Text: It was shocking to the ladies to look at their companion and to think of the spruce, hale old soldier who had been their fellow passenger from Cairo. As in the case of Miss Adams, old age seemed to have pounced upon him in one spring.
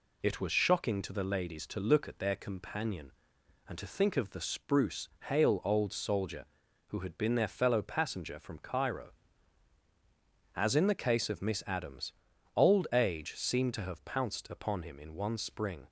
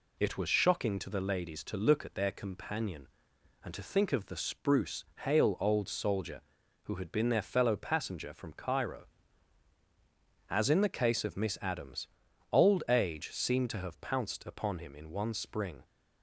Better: neither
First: none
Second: none

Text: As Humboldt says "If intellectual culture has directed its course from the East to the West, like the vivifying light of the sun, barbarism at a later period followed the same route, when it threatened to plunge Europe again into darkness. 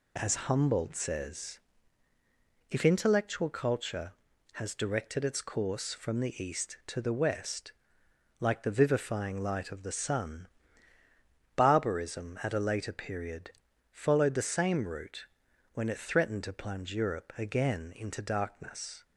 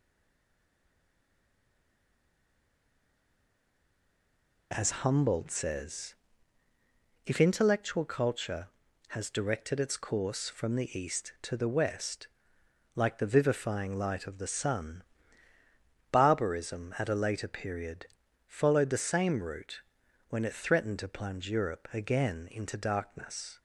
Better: first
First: pauses between "says" and "If"; at 1.5 s; 1.1 s long // pauses between "period" and "followed"; at 13.5 s; 0.42 s long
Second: stays silent before the first word; strong; until 4.7 s; 4.7 s long // pauses between "says" and "If"; at 6.1 s; 1.1 s long // pauses between "period" and "followed"; at 18.0 s; 0.42 s long

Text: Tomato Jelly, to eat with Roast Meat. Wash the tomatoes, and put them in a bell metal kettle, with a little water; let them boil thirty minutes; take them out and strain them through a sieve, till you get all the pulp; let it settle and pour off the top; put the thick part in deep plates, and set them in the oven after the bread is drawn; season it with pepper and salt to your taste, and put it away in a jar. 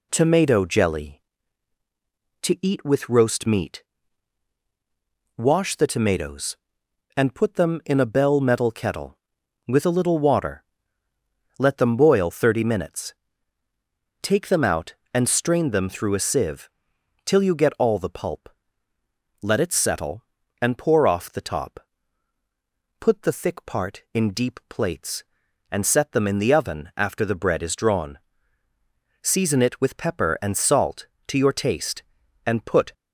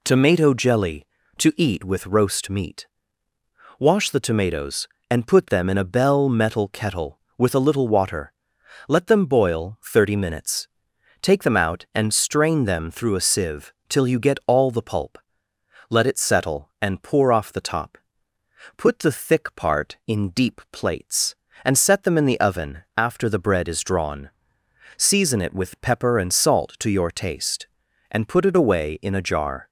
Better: second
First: stops before "it away in a jar"; at 32.9 s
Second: none

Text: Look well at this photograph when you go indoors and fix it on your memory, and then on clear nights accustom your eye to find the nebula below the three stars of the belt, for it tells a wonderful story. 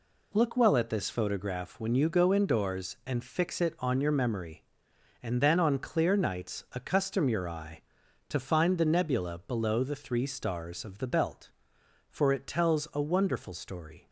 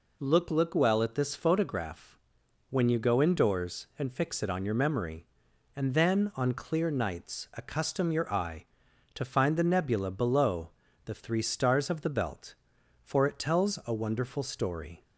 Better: first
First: none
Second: says "Look" twice; at 0.4 s // pauses between "photograph" and "when"; noticeable; at 2.1 s; 0.54 s long // pauses between "below" and "the"; slight; at 10.7 s; 0.34 s long

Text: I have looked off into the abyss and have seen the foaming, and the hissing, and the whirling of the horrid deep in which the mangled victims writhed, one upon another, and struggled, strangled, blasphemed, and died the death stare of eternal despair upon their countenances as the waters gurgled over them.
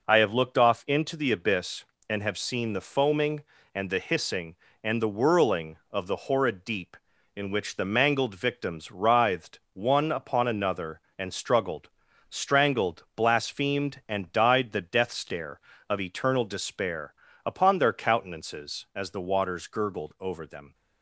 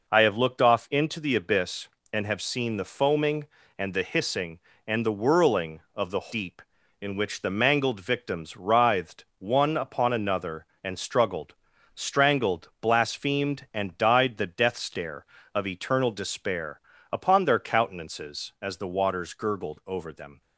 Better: first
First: pauses between "despair" and "upon"; slight; at 17.1 s; 0.32 s long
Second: skips "horrid"; at 6.2 s // pauses between "despair" and "upon"; slight; at 16.8 s; 0.32 s long

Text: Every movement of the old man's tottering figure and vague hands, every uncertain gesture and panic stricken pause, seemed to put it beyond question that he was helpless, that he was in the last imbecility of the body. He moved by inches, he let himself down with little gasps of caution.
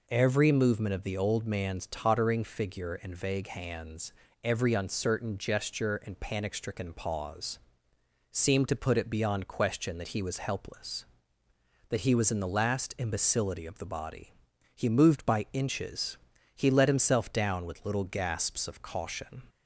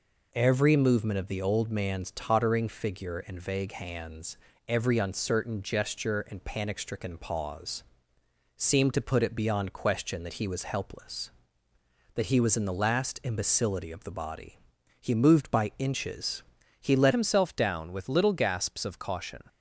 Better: first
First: none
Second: changes voice at "himself"; from 17.1 s on; 2.3 s long

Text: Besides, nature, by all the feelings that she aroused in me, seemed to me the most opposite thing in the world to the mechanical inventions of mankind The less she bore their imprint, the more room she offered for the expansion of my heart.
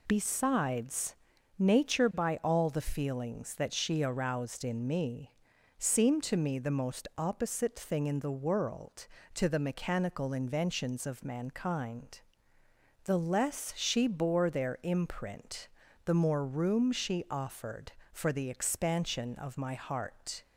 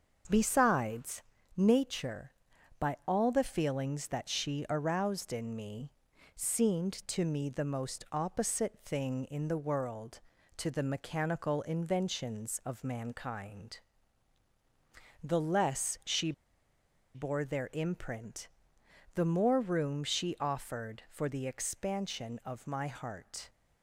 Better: first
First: pauses between "mankind" and "The"; noticeable; at 12.2 s; 0.84 s long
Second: starts louder than the rest; until 1.6 s; 6.5 dB // pauses between "mankind" and "The"; strong; at 13.7 s; 1.4 s long // pauses between "she" and "bore"; noticeable; at 16.3 s; 0.82 s long

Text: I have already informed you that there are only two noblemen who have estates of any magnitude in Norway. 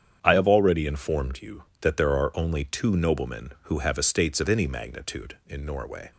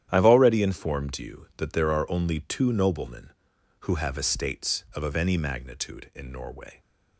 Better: first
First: starts louder than the rest; strong; until 1.2 s; 8.5 dB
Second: starts louder than the rest; strong; until 1.1 s; 10.5 dB // says "of" twice; at 5.0 s

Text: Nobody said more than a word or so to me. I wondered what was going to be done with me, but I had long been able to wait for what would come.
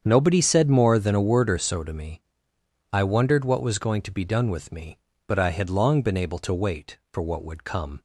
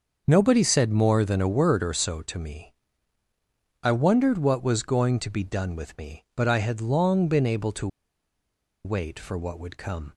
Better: first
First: starts louder than the rest; strong; until 1.0 s; 7.5 dB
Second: starts louder than the rest; until 1.2 s; 6 dB // pauses between "to" and "wait"; noticeable; at 7.8 s; 0.97 s long

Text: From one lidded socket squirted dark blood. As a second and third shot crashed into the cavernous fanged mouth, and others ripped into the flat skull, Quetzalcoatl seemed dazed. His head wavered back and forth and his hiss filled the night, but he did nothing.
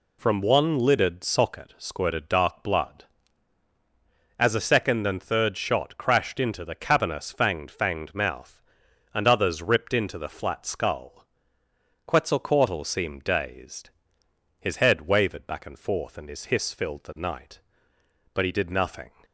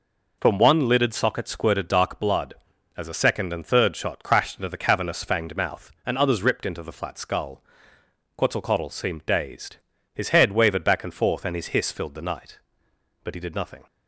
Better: second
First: says "fanged" twice; at 7.7 s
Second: none

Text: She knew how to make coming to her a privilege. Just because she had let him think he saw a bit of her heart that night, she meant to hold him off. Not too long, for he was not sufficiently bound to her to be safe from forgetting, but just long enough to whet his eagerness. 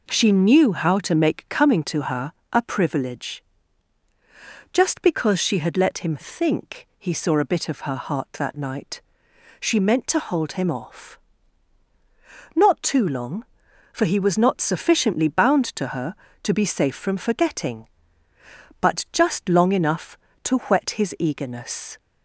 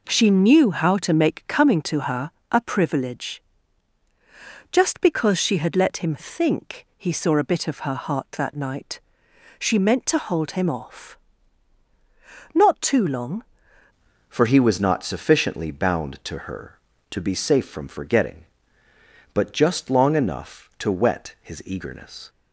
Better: first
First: pauses between "her" and "a"; slight; at 2.3 s; 0.19 s long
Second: pauses between "her" and "a"; slight; at 2.3 s; 0.20 s long // changes voice at "for"; from 14.2 s on; 8.0 s long

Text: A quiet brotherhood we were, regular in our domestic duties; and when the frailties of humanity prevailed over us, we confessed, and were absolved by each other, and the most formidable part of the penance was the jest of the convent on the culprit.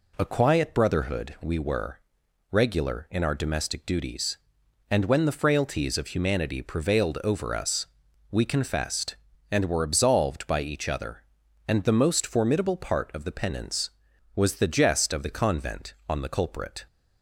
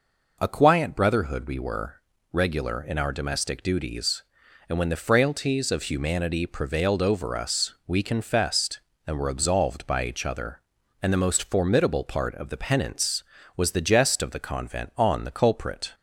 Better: neither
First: none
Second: none

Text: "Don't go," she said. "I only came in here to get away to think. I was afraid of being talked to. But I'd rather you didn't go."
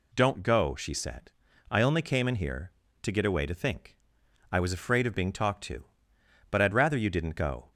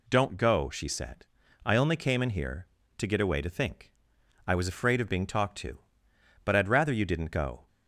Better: neither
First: none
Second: none

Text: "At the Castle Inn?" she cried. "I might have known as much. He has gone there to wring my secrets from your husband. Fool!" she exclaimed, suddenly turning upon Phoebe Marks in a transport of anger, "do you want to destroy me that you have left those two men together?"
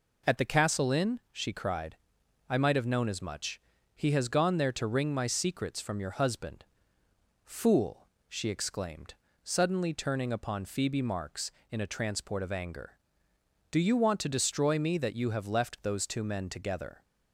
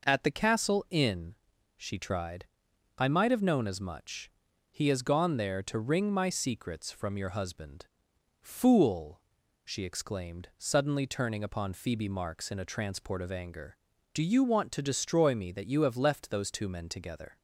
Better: first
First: none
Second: says "tried" for "cried"; at 1.9 s

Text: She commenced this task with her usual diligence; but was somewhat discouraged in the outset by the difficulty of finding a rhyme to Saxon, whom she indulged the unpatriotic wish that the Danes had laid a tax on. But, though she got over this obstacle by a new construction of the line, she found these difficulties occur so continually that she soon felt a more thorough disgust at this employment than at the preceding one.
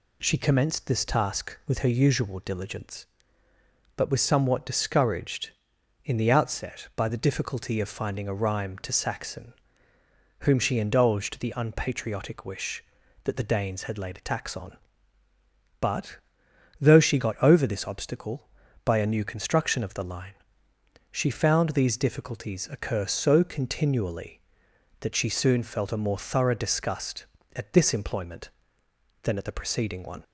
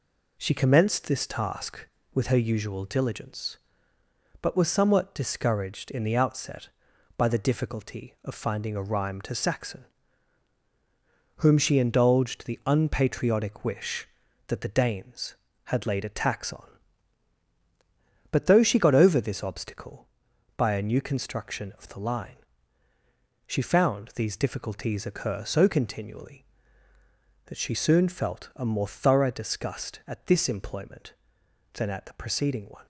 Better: neither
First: none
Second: none

